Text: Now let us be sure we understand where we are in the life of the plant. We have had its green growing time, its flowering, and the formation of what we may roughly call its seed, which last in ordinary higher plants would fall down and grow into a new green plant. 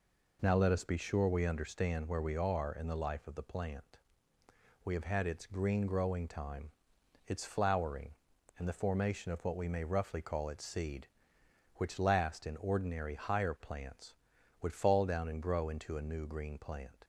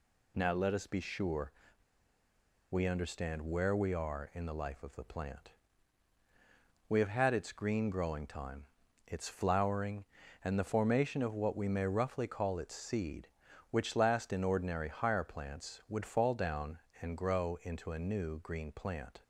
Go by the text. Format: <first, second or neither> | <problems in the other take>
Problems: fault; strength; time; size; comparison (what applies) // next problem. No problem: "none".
first | pauses between "sure" and "we"; at 1.5 s; 1.1 s long